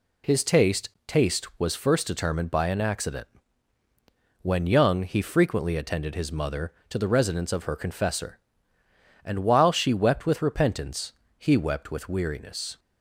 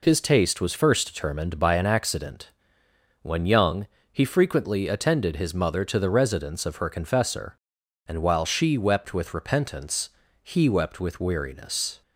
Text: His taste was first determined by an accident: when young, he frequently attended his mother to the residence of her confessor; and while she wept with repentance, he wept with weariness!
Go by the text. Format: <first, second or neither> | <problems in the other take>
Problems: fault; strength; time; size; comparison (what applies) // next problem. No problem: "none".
second | says "taste" twice; at 1.0 s